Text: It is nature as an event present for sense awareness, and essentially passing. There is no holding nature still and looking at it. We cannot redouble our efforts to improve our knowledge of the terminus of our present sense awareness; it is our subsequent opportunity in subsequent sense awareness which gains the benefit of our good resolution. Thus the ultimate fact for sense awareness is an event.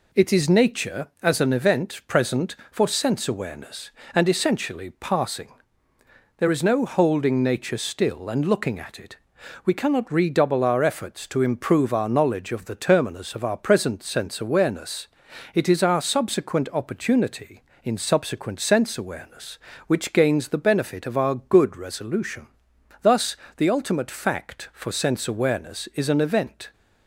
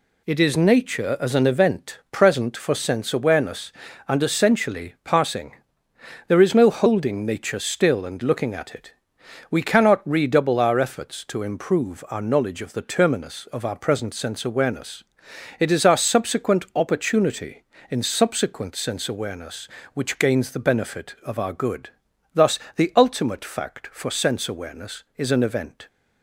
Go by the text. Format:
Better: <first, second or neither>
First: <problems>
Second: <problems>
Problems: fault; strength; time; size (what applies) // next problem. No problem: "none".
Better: first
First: pauses between "Thus" and "the"; slight; at 23.3 s; 0.22 s long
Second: skips "resolution"; at 22.1 s // pauses between "Thus" and "the"; slight; at 22.5 s; 0.16 s long